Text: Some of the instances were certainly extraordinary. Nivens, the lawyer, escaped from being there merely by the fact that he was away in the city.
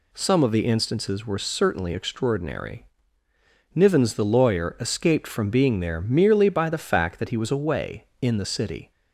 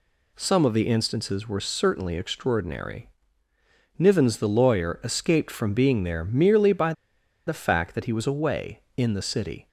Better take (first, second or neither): first